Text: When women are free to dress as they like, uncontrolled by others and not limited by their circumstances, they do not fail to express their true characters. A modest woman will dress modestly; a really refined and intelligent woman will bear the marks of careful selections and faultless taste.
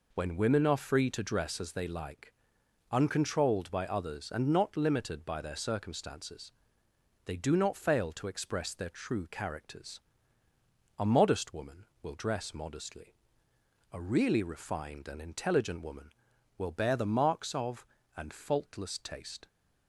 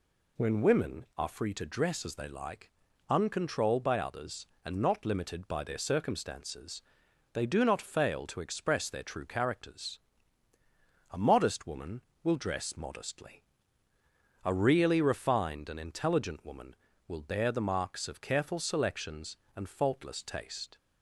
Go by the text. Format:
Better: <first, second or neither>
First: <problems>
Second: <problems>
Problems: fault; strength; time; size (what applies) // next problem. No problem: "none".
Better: second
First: skips "careful selections"; at 17.9 s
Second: none